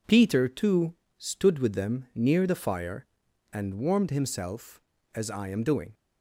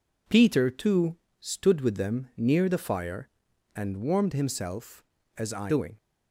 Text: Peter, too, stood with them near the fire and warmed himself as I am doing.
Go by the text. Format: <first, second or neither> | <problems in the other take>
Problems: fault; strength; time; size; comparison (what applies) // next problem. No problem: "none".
first | skips "am"; at 5.7 s